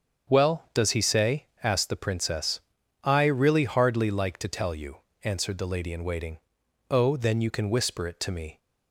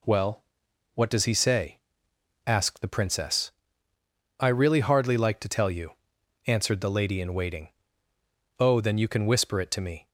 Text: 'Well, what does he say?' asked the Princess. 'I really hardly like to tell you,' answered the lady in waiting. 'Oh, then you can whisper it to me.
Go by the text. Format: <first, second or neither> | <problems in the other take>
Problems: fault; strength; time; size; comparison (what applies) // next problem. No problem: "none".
second | starts louder than the rest; strong; until 1.4 s; 7 dB // skips "what"; at 0.6 s